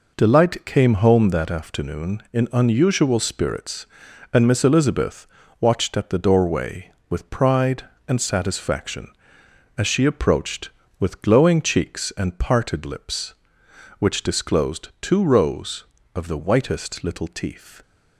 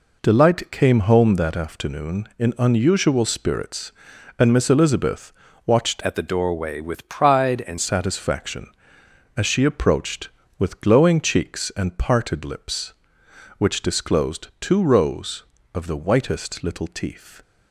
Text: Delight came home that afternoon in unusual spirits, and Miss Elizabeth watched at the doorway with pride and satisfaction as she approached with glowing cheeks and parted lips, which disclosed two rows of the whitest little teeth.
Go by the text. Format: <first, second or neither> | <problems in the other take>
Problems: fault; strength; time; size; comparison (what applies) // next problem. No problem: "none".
first | pauses between "Elizabeth" and "watched"; slight; at 5.3 s; 0.34 s long; slight in the first // changes voice from "at" to "and"; from 6.0 to 7.7 s; 1.7 s long